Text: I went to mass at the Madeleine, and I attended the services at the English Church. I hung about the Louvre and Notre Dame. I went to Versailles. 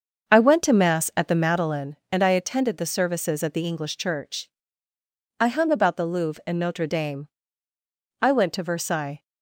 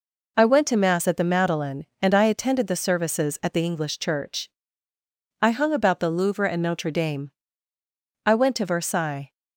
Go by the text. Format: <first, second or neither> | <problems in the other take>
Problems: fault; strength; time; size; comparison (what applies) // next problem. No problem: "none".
second | starts louder than the rest; until 1.8 s; 6.5 dB